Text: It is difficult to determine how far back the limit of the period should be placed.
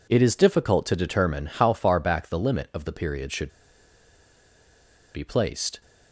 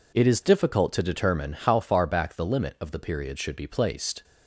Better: second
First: pauses between "should" and "be"; strong; at 3.5 s; 1.6 s long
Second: none

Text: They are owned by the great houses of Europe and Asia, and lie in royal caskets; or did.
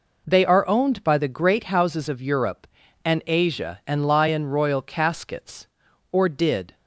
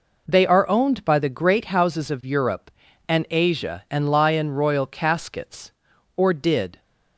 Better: neither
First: none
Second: none

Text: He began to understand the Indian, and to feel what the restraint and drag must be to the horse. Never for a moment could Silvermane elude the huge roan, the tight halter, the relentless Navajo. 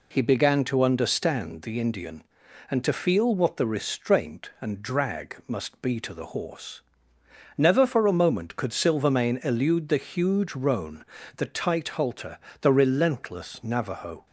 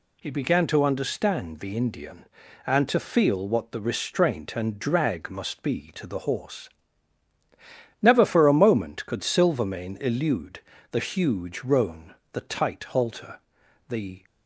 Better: first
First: none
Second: pauses between "elude" and "the"; slight; at 10.5 s; 0.30 s long // stops before "relentless Navajo"; at 14.2 s

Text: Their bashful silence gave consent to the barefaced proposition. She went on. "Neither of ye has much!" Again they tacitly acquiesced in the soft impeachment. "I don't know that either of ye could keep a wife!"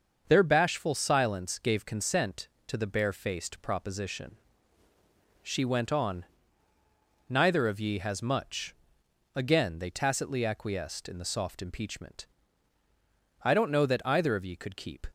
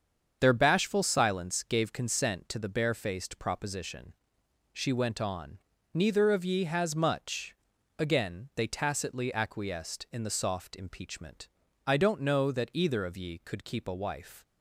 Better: second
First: starts louder than the rest; until 1.2 s; 6.5 dB // stops before "a wife"; at 15.0 s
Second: starts louder than the rest; strong; until 1.4 s; 7 dB

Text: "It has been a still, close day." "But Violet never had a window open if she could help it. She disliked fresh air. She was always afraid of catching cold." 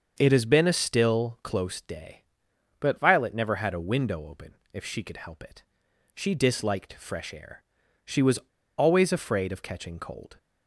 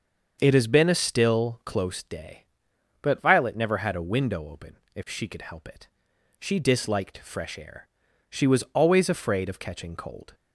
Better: second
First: starts louder than the rest; until 1.1 s; 6.5 dB // pauses between "open" and "if"; slight; at 4.5 s; 0.18 s long // pauses between "was" and "always"; at 8.3 s; 0.38 s long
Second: starts louder than the rest; until 1.4 s; 6.5 dB // pauses between "open" and "if"; slight; at 4.7 s; 0.18 s long

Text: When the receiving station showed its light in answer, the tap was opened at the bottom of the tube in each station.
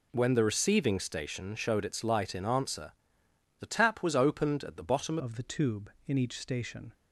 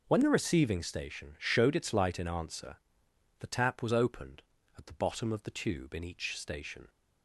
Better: second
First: changes voice at "of"; from 5.1 s on; 1.8 s long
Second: none

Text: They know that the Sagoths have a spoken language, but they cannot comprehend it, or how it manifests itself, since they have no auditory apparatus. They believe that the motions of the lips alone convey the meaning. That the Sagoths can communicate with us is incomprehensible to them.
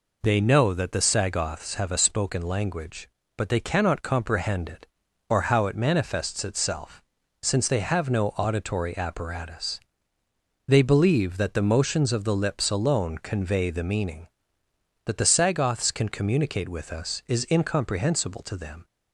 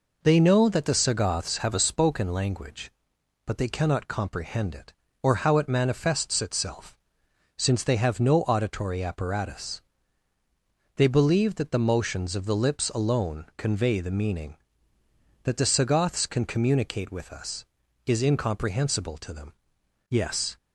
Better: first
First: none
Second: goes on to say "Yes"; slight; from 20.1 s on; 0.46 s long

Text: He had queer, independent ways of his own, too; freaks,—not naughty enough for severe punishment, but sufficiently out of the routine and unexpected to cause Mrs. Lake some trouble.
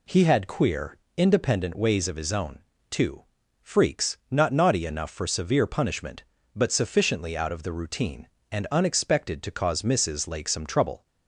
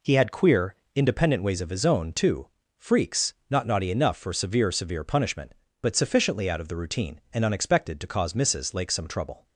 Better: first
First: none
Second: says "severe" twice; at 4.7 s

